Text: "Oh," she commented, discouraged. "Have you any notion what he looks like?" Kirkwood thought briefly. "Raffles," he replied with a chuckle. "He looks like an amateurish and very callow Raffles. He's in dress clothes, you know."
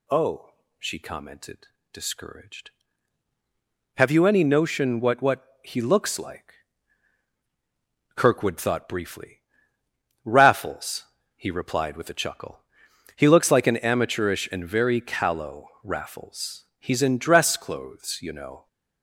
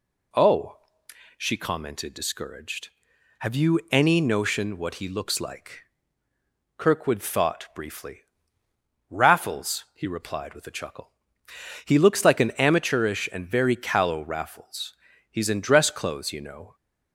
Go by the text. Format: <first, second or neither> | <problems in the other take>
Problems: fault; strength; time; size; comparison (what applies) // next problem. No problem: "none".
second | says "what" twice; at 5.2 s